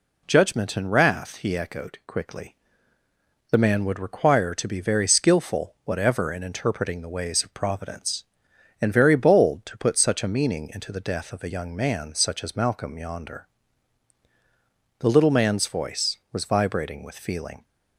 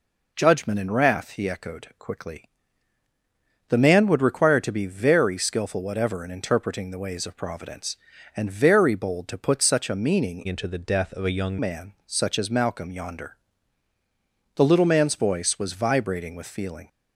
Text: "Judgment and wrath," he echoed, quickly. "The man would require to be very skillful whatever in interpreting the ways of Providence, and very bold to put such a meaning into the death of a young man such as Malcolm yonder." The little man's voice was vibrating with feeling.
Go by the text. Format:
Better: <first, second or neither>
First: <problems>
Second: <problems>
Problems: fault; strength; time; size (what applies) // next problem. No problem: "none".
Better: first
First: none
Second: changes voice from "into" to "young"; from 10.4 to 11.5 s; 1.1 s long